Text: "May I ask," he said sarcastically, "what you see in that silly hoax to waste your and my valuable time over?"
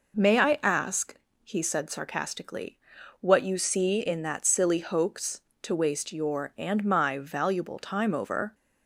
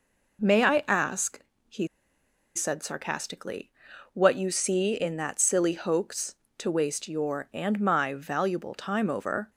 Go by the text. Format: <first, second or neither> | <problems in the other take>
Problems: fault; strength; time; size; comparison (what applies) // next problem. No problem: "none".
first | pauses between "he" and "said"; noticeable; at 1.8 s; 0.69 s long